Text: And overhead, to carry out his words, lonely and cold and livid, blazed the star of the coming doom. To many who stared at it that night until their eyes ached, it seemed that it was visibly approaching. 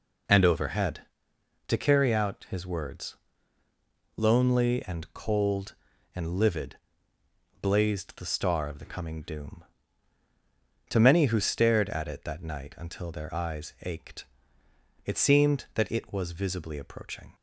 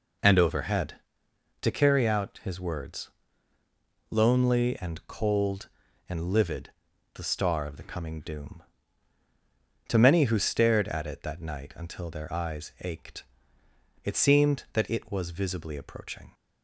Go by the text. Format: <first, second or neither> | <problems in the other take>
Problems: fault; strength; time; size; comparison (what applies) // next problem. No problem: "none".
first | skips "blazed"; at 6.9 s